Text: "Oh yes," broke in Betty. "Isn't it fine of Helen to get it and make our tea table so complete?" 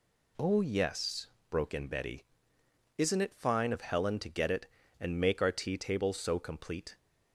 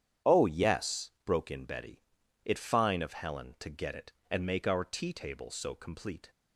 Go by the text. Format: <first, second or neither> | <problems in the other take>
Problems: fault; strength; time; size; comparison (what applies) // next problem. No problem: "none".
first | starts louder than the rest; strong; until 1.3 s; 9 dB // skips "Isn't"; at 2.2 s